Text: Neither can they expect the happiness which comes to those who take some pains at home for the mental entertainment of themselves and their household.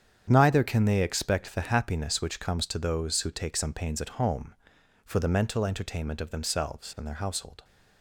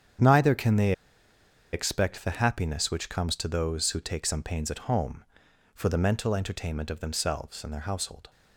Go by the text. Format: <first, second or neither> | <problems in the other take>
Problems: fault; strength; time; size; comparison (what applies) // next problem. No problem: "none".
first | starts louder than the rest; strong; until 2.0 s; 8.5 dB; strong in the first // pauses between "they" and "expect"; noticeable; at 0.9 s; 0.81 s long